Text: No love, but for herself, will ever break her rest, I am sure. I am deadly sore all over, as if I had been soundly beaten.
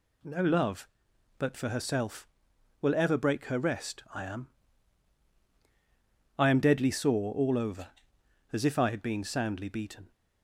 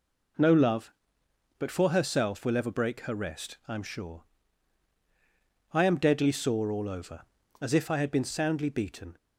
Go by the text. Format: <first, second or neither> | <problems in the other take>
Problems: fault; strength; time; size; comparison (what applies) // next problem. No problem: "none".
second | skips "sure"; at 5.4 s